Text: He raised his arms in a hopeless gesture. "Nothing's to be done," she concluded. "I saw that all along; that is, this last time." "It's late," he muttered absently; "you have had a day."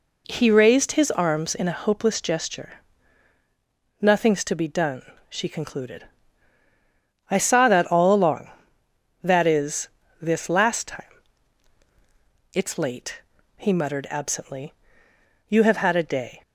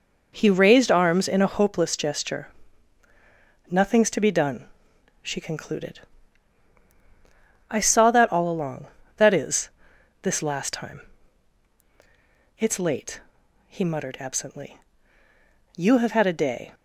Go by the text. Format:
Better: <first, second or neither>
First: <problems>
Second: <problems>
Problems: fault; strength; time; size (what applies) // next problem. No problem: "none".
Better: first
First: none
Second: skips "his"; at 0.8 s